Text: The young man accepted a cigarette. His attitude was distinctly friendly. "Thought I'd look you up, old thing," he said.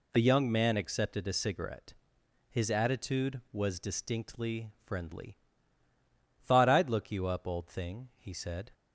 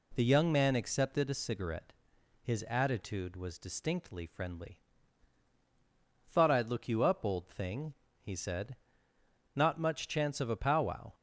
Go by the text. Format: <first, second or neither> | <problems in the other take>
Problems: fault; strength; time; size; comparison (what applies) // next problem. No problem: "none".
first | goes on to say "Not much chance of a powwow"; from 9.5 s on; 1.5 s long